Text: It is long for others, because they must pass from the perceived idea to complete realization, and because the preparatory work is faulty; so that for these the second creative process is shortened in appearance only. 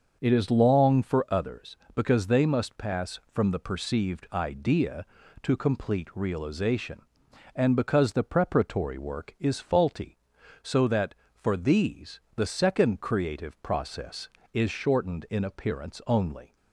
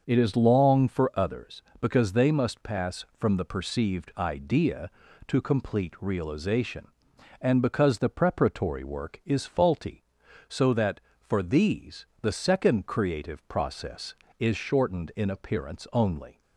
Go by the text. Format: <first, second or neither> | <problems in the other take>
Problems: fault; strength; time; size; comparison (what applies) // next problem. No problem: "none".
neither | starts louder than the rest; the same in both